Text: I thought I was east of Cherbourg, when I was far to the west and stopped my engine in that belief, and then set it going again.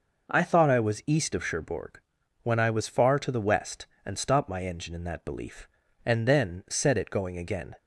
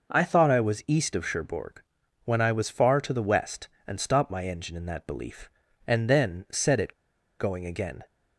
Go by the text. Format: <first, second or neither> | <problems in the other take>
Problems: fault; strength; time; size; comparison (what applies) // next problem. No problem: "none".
first | pauses between "it" and "going"; noticeable; at 6.9 s; 0.46 s long